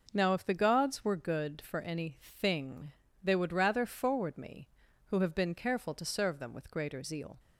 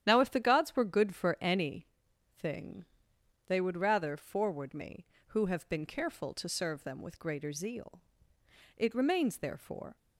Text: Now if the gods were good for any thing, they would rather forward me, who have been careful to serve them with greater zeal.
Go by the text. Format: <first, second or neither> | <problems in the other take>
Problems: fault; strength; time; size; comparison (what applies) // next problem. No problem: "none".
first | starts louder than the rest; strong; until 1.0 s; 10.5 dB // pauses between "any" and "thing"; noticeable; at 1.8 s; 0.52 s long // goes on to say "It remains therefore"; noticeable; from 8.7 s on; 1.1 s long